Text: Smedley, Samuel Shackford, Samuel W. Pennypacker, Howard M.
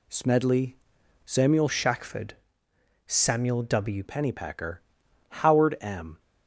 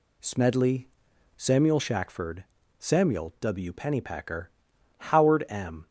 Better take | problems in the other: second | changes voice from "Shackford" to "W"; from 1.6 to 4.0 s; 2.4 s long

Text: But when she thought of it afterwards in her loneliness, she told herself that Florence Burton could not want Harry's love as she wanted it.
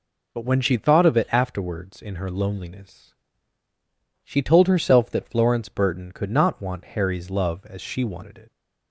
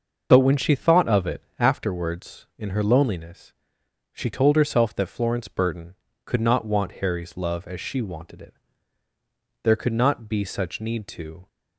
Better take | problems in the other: first | starts louder than the rest; noticeable; until 1.3 s; 6 dB // pauses between "it" and "afterwards"; slight; at 1.4 s; 0.16 s long // goes on to say "There could not be such need to"; strong; from 9.6 s on; 1.8 s long

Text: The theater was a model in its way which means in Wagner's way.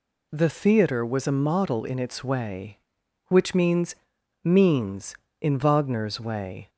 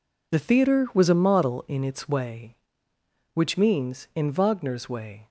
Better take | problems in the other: second | says "means" twice; at 4.4 s

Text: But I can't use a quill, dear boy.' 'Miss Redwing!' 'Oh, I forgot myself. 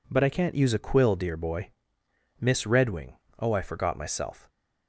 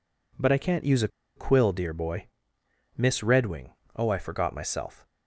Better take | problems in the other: first | pauses between "a" and "quill"; slight; at 1.0 s; 0.28 s long

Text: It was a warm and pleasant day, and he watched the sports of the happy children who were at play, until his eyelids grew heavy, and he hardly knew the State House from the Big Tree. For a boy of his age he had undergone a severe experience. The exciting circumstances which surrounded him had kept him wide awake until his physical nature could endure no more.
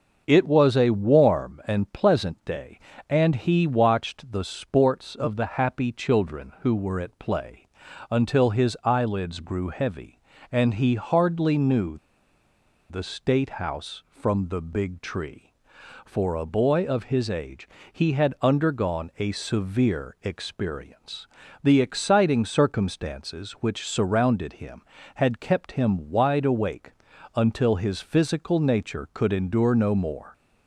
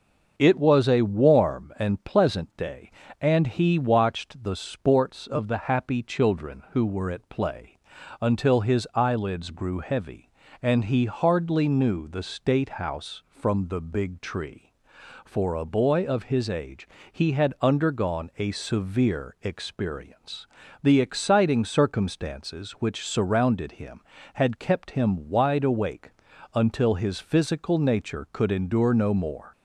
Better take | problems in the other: second | starts louder than the rest; until 1.2 s; 6.5 dB; also in the second // pauses between "knew" and "the"; noticeable; at 11.9 s; 0.92 s long // pauses between "age" and "he"; slight; at 17.6 s; 0.24 s long; slight in the second // pauses between "awake" and "until"; noticeable; at 26.8 s; 0.46 s long; noticeable in the second

